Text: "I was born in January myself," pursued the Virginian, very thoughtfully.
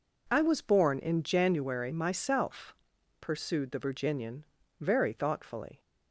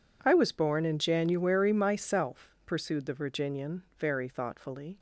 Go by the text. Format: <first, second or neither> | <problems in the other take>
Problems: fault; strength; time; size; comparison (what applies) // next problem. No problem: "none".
neither | none